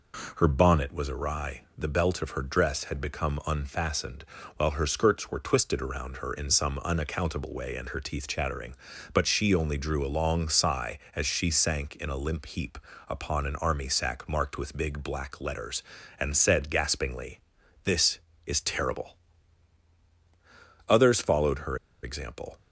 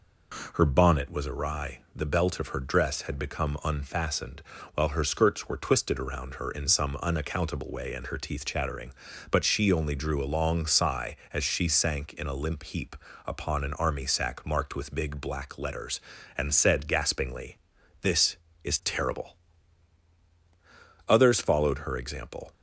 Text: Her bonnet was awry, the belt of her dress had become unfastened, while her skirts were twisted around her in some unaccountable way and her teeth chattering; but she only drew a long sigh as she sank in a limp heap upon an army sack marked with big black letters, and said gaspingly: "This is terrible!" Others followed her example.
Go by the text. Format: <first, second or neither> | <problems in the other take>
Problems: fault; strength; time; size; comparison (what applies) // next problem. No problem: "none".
second | pauses between "heap" and "upon"; slight; at 12.7 s; 0.30 s long; slight in the second // pauses between "her" and "example"; slight; at 21.7 s; 0.26 s long